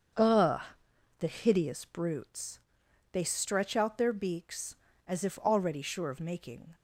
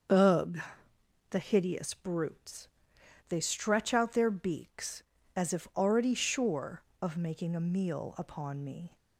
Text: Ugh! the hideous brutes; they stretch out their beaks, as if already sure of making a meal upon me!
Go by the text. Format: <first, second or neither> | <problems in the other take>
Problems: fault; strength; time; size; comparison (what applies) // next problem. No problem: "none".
second | starts louder than the rest; until 1.7 s; 7 dB; also in the second // stops before "a meal upon me"; at 6.7 s